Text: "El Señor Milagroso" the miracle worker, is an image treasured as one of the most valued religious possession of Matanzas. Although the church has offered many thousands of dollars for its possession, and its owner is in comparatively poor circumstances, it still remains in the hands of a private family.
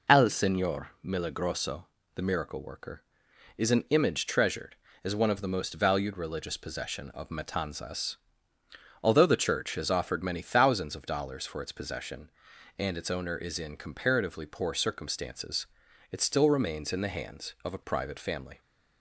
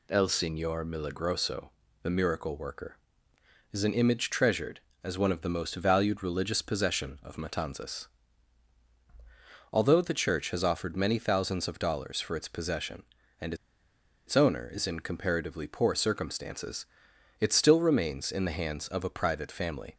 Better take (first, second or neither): first